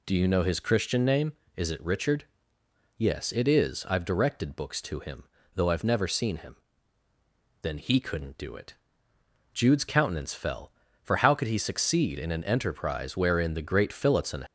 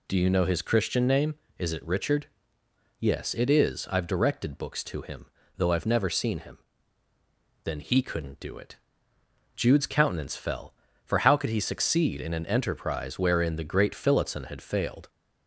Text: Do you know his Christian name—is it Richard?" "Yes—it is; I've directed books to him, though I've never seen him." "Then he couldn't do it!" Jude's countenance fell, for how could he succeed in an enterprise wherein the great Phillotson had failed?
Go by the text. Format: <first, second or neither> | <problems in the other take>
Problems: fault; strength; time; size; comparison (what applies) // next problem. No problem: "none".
second | stops before "had failed"; at 14.4 s